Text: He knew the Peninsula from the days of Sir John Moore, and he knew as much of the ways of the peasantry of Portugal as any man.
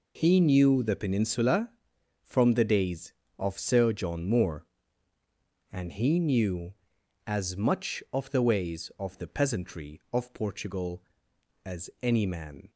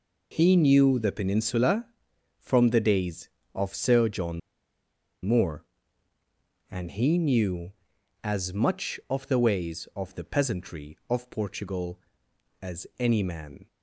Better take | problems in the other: first | pauses between "John" and "Moore"; noticeable; at 4.3 s; 0.84 s long

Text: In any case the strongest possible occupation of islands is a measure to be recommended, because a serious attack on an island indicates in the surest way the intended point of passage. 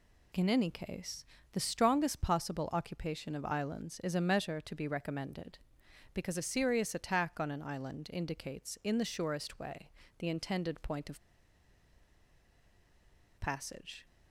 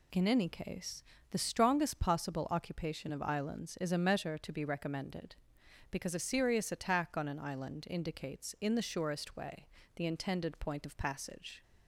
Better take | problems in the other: second | pauses between "case" and "the"; slight; at 1.2 s; 0.26 s long; slight in the second // pauses between "way" and "the"; slight; at 9.9 s; 0.30 s long; slight in the second // pauses between "of" and "passage"; strong; at 11.1 s; 2.1 s long

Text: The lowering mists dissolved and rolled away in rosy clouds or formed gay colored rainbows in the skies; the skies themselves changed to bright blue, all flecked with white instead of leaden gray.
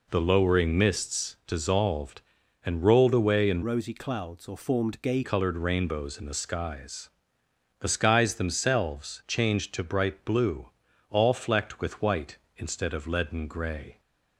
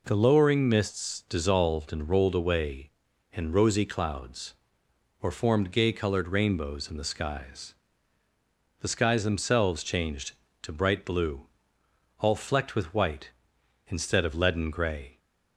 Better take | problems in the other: second | changes voice from "rosy" to "gay"; from 3.6 to 5.2 s; 1.6 s long

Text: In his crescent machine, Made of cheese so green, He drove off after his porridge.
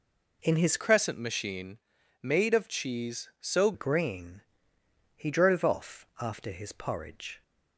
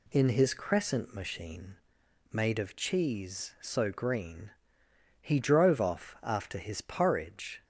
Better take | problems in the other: second | changes voice from "crescent" to "so"; from 0.7 to 3.7 s; 3.0 s long

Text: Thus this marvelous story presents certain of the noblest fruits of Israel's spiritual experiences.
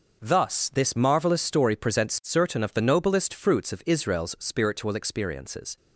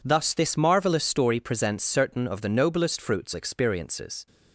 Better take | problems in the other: first | skips "of Israel's spiritual"; at 3.3 s

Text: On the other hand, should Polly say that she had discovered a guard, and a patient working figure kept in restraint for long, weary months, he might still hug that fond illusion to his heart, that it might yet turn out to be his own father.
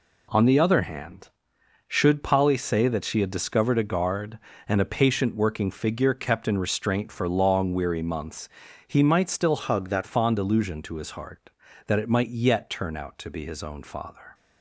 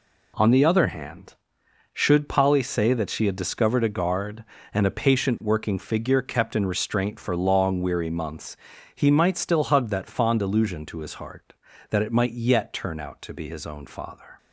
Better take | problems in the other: second | changes voice from "hug" to "that"; from 9.5 to 10.0 s; 0.5 s long

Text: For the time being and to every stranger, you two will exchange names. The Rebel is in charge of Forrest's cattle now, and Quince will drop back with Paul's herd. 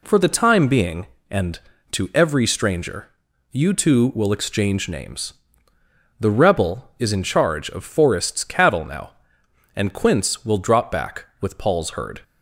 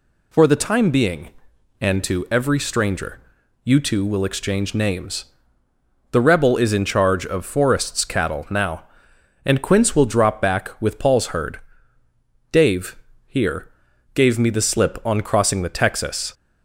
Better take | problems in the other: first | goes on to say "Dave here gave me the slip on crossing the Texas"; strong; from 12.5 s on; 3.8 s long

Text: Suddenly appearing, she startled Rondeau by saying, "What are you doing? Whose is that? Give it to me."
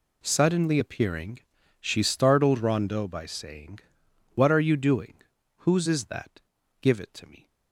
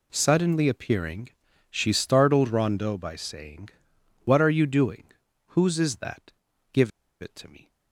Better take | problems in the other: first | pauses between "Give" and "it"; slight; at 6.9 s; 0.30 s long

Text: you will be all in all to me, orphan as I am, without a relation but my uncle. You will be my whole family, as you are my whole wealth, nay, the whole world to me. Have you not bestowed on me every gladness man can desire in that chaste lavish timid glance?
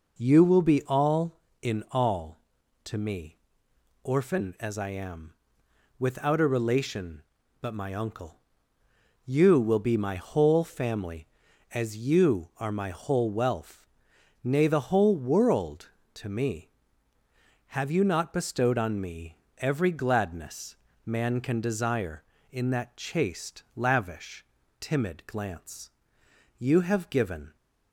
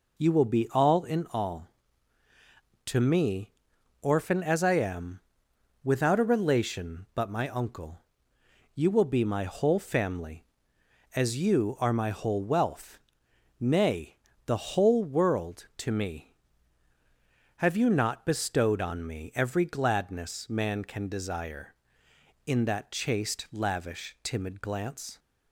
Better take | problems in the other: second | pauses between "me" and "every"; slight; at 19.3 s; 0.22 s long // pauses between "gladness" and "man"; slight; at 20.7 s; 0.28 s long // pauses between "lavish" and "timid"; slight; at 24.4 s; 0.34 s long // goes on to say "You have given"; noticeable; from 26.5 s on; 0.98 s long

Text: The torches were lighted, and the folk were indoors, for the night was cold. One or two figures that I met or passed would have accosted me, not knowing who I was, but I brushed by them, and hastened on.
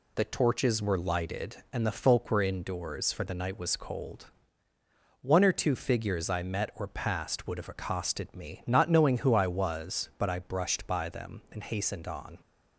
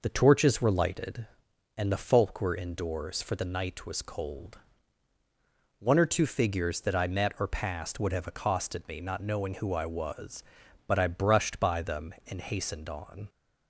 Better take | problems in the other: second | skips "that"; at 6.2 s

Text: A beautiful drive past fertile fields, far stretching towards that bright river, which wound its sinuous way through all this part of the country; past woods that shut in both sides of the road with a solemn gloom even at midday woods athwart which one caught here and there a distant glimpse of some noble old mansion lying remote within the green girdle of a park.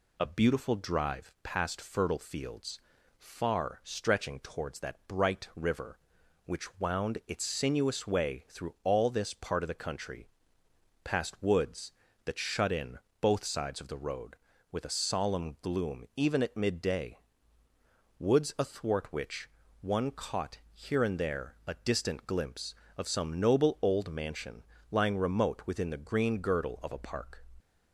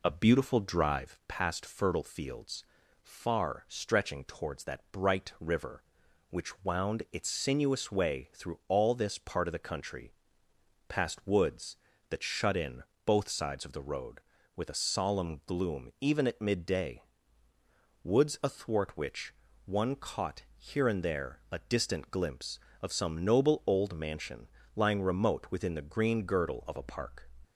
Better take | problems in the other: first | starts louder than the rest; slight; until 1.4 s; 3.5 dB // pauses between "in" and "both"; slight; at 12.8 s; 0.24 s long; slight in the first // pauses between "midday" and "woods"; at 17.0 s; 1.0 s long; also in the first // pauses between "which" and "one"; slight; at 19.3 s; 0.32 s long; slight in the first // pauses between "mansion" and "lying"; slight; at 24.4 s; 0.28 s long; slight in the first

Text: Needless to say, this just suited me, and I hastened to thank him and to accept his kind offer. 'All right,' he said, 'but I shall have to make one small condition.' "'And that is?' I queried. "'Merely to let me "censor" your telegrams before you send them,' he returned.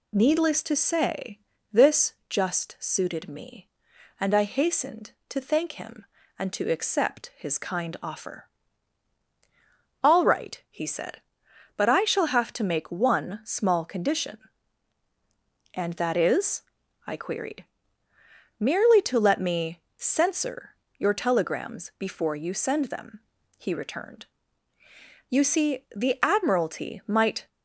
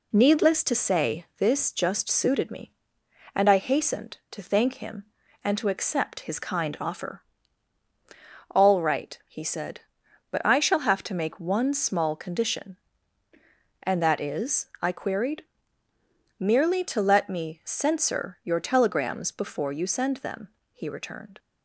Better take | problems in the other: second | pauses between "this" and "just"; slight; at 2.1 s; 0.18 s long // pauses between "censor" and "your"; slight; at 20.7 s; 0.20 s long // goes on to say "You see the Admiralty might"; strong; from 25.2 s on; 2.2 s long

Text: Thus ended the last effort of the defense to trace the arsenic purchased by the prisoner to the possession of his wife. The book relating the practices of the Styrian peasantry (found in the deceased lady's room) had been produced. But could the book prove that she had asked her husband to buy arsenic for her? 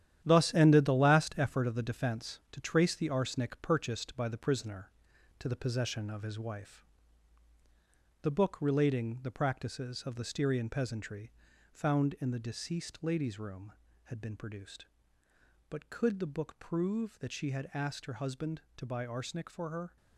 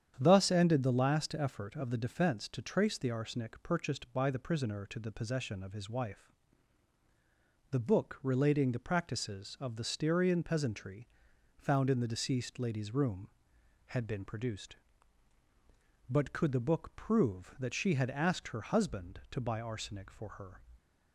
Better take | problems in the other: second | gets quieter; strong; throughout; 8.5 dB // starts louder than the rest; strong; until 1.2 s; 11 dB; strong in the second

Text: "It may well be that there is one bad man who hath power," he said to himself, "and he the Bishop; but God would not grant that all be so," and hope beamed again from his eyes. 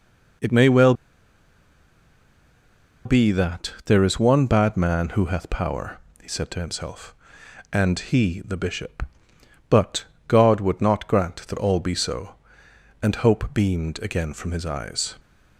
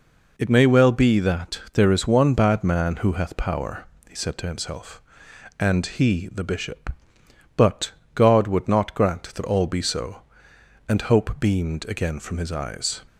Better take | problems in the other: second | pauses between "well" and "be"; strong; at 0.9 s; 2.1 s long // pauses between "but" and "God"; slight; at 10.0 s; 0.22 s long; slight in the second

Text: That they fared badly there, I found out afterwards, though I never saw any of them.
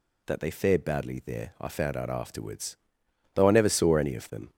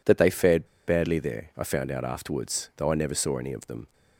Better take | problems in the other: first | pauses between "fared" and "badly"; slight; at 0.6 s; 0.20 s long

